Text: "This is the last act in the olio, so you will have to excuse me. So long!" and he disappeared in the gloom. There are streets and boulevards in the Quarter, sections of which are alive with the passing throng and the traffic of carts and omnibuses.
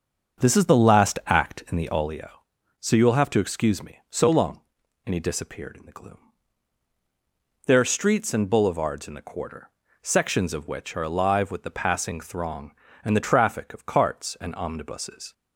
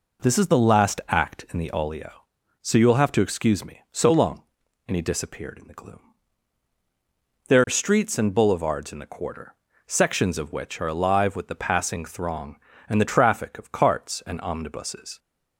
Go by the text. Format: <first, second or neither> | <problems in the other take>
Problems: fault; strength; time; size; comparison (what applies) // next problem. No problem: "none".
second | starts louder than the rest; until 2.3 s; 6.5 dB